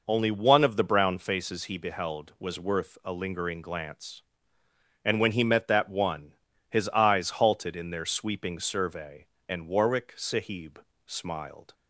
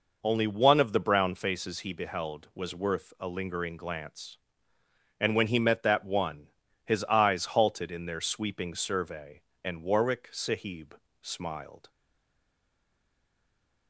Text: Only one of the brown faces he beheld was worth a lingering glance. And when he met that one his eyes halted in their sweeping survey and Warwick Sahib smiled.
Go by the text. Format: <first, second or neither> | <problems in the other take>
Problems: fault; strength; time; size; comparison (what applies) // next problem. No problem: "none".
first | pauses between "one" and "his"; at 6.4 s; 0.38 s long; also in the first // pauses between "Sahib" and "smiled"; slight; at 10.9 s; 0.24 s long; slight in the first // stays silent after the last word; noticeable; from 11.8 s on; 2.0 s long